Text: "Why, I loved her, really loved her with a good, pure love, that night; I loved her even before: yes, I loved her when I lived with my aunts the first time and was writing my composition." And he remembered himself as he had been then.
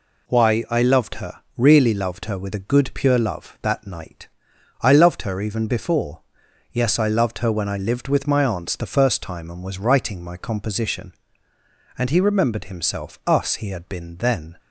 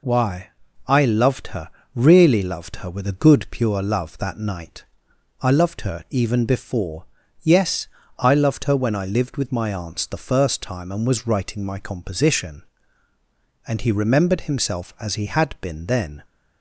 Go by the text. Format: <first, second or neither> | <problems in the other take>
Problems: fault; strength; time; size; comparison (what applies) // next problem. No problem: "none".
second | says "us" for "as"; at 13.2 s